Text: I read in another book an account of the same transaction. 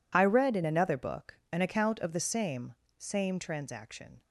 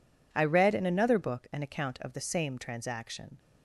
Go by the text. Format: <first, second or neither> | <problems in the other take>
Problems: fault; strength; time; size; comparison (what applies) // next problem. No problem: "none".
second | says "same" twice; at 2.9 s